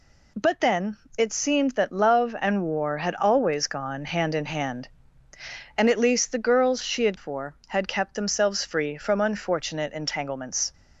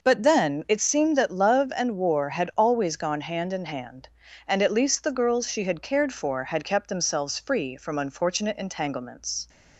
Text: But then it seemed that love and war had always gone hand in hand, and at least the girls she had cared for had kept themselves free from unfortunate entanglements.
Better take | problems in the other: second | pauses between "then" and "it"; slight; at 0.9 s; 0.22 s long // skips "cared"; at 7.1 s

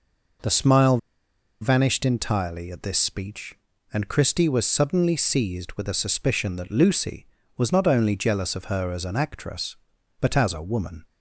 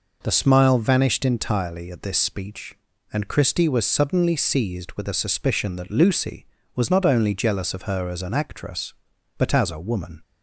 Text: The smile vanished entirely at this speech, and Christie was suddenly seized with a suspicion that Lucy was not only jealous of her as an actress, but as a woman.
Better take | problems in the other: second | pauses between "smile" and "vanished"; noticeable; at 0.9 s; 0.63 s long

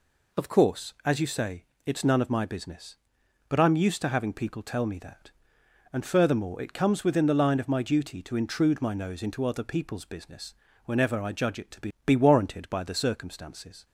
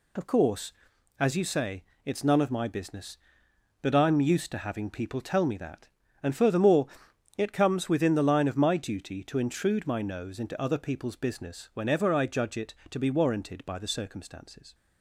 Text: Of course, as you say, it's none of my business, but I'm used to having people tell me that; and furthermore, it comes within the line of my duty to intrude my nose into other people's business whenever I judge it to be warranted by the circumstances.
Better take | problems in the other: second | pauses between "business" and "whenever"; slight; at 10.5 s; 0.30 s long // says "be" twice; at 12.0 s

